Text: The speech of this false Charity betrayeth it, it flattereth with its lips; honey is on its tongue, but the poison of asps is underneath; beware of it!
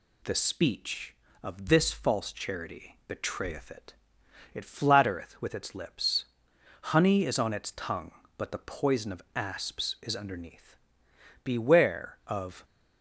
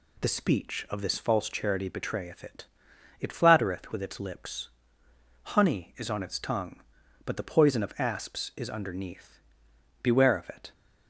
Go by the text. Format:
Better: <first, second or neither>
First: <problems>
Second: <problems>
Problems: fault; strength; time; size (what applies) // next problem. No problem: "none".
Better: second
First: stops before "it"; at 12.6 s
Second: none